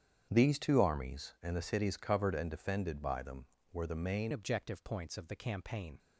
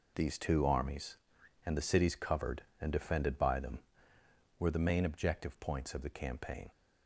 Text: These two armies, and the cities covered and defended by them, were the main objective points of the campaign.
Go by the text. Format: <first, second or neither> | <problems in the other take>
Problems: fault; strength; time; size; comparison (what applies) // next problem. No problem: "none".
second | starts louder than the rest; strong; until 1.3 s; 8.5 dB // changes voice at "objective"; from 4.3 s on; 1.6 s long